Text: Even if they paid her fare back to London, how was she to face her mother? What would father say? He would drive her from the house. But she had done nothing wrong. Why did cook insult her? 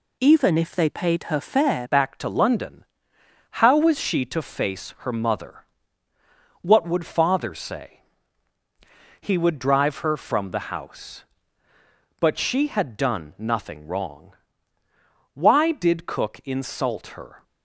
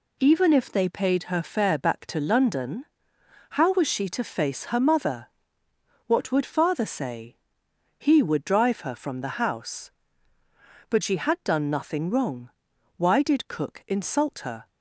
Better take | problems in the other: second | changes voice at "back"; from 1.9 s on; 15.5 s long

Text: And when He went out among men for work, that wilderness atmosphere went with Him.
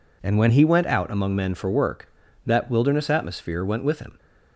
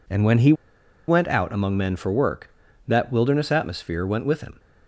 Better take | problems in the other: first | pauses between "He" and "went"; noticeable; at 0.5 s; 0.55 s long

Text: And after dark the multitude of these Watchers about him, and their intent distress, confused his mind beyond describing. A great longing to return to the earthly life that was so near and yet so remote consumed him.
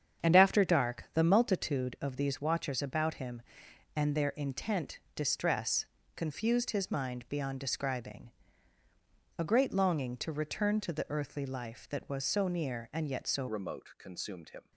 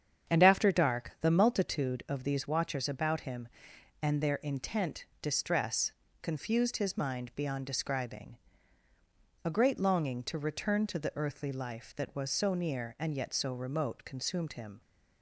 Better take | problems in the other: second | starts louder than the rest; strong; until 1.3 s; 8 dB; strong in the second // pauses between "intent" and "distress"; slight; at 4.9 s; 0.18 s long; slight in the second // changes voice at "remote"; from 13.4 s on; 1.3 s long

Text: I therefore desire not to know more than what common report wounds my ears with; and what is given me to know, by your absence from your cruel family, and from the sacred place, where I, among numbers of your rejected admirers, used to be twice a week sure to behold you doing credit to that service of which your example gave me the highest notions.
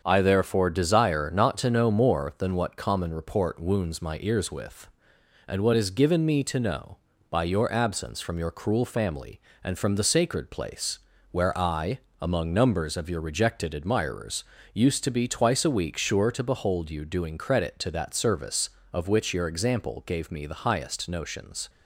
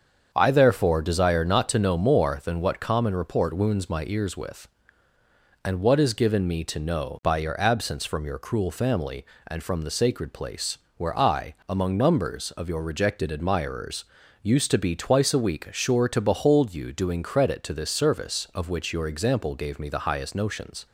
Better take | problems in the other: first | starts louder than the rest; until 1.3 s; 7 dB; also in the first // says "this" for "that"; at 17.7 s

